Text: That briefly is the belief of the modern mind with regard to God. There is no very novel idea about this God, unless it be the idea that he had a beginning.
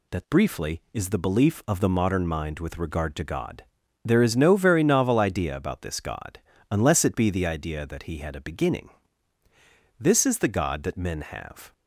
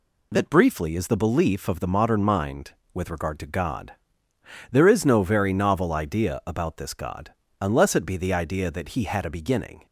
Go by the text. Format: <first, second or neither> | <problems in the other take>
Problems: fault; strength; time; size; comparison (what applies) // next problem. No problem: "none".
second | goes on to say "This is the God that men have"; strong; from 10.0 s on; 1.7 s long